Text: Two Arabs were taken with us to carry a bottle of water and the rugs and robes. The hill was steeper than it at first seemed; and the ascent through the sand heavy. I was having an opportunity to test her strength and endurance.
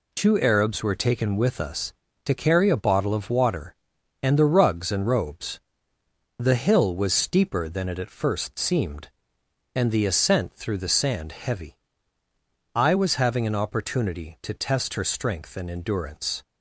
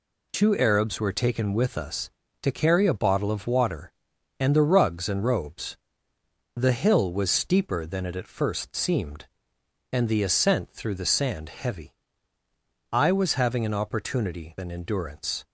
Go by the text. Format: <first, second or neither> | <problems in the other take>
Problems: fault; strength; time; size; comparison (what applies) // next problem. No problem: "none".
first | skips "to test her strength"; at 14.5 s